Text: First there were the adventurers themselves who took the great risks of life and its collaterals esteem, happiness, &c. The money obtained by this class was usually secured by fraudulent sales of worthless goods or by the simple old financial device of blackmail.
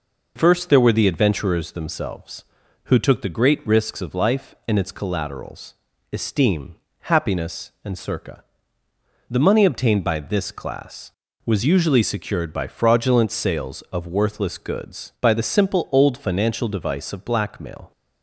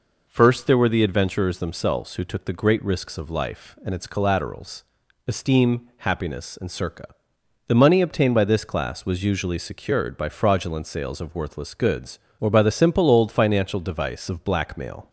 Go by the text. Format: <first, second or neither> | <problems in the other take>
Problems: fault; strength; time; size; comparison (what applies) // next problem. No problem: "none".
second | pauses between "collaterals" and "esteem"; at 5.7 s; 0.40 s long; also in the second // skips "or"; at 15.1 s